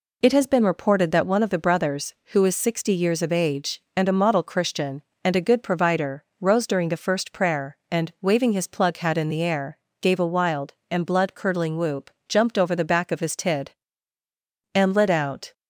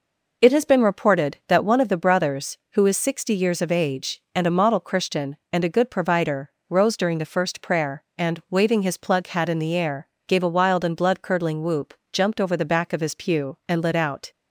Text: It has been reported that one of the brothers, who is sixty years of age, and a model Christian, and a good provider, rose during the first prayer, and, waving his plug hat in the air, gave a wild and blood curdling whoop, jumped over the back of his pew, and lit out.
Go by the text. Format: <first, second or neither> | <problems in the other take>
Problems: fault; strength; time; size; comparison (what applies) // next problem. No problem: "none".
second | says "tid" for "pew"; at 13.3 s